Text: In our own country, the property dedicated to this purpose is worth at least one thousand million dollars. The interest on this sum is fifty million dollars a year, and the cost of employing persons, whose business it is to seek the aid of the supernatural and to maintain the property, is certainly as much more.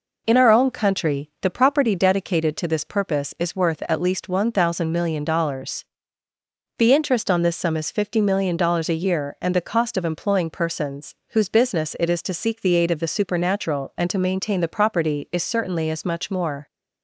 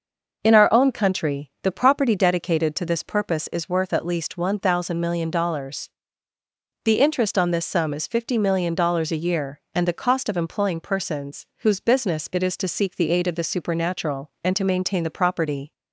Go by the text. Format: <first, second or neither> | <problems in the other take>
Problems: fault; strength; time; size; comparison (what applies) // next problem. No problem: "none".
first | starts louder than the rest; noticeable; until 1.4 s; 6 dB // stops before "is certainly as much more"; at 15.7 s